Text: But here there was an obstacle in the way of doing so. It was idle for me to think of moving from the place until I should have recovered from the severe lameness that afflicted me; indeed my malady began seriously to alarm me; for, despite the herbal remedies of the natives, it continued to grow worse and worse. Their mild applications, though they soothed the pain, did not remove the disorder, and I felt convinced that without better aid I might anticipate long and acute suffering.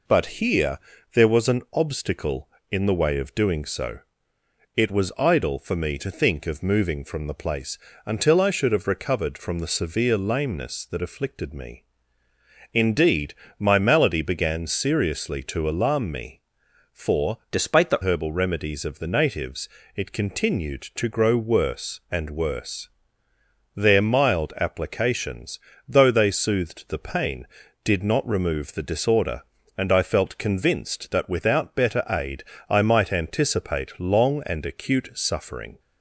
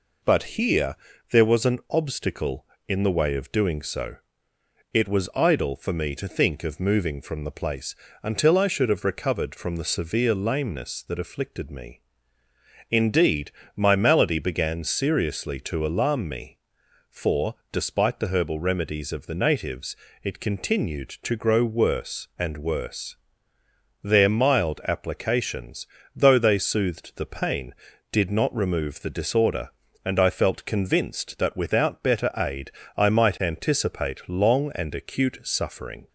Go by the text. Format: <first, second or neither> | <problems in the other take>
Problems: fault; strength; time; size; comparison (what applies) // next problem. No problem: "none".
second | pauses between "here" and "there"; slight; at 0.7 s; 0.36 s long; slight in the second // pauses between "place" and "until"; slight; at 7.7 s; 0.28 s long; slight in the second // pauses between "indeed" and "my"; slight; at 13.3 s; 0.24 s long; slight in the second // changes voice from "despite" to "the"; from 17.5 to 17.9 s; 0.4 s long // pauses between "aid" and "I"; slight; at 32.4 s; 0.24 s long; slight in the second